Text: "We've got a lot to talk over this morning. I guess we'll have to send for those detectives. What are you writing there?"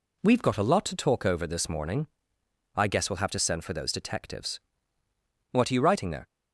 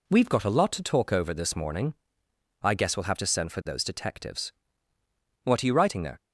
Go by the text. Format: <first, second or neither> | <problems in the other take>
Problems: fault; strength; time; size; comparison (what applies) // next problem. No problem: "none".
neither | none